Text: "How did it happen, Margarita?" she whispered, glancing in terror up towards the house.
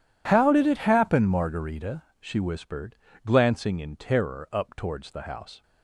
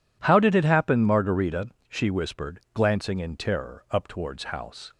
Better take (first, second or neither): first